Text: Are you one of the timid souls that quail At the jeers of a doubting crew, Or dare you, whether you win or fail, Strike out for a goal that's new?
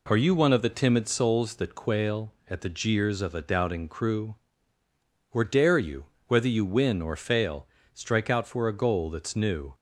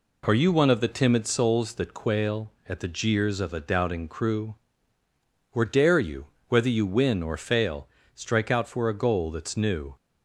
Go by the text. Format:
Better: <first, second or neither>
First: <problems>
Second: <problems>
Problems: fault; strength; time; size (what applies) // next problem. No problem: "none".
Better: neither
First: none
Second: none